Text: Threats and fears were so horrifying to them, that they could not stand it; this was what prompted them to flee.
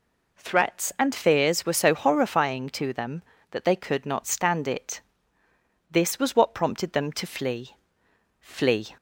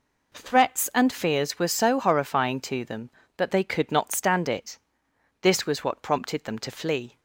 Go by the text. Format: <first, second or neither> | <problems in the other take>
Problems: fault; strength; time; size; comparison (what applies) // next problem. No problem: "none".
second | says "flee" twice; at 8.4 s